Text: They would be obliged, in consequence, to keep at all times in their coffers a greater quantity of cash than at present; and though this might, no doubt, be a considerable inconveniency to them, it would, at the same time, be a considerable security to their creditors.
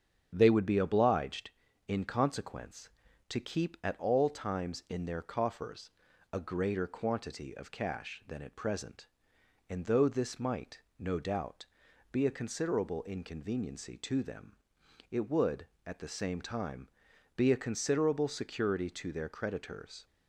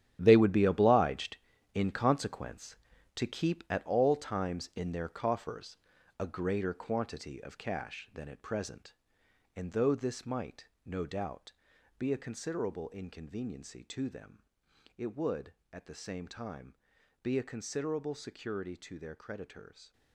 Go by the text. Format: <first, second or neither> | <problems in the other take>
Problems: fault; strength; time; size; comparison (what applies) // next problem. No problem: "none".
first | gets quieter; strong; throughout; 11.5 dB // starts louder than the rest; strong; until 1.2 s; 10.5 dB; strong in the first // pauses between "coffers" and "a"; at 5.7 s; 0.40 s long; also in the first